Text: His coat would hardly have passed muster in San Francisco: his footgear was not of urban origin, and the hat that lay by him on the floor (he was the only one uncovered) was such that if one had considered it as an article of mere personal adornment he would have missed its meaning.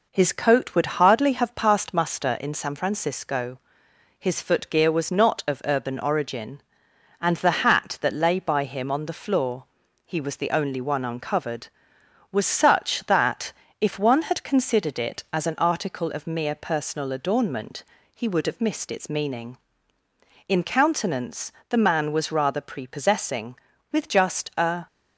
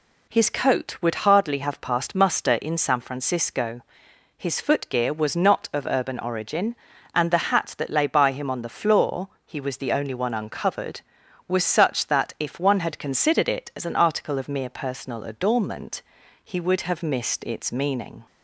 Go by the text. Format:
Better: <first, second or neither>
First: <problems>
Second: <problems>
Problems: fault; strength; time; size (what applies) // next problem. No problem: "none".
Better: second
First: pauses between "that" and "if"; slight; at 13.5 s; 0.28 s long // pauses between "adornment" and "he"; slight; at 17.8 s; 0.32 s long // goes on to say "In countenance the man was rather prepossessing with just a"; strong; from 20.4 s on; 4.4 s long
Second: pauses between "adornment" and "he"; at 16.0 s; 0.42 s long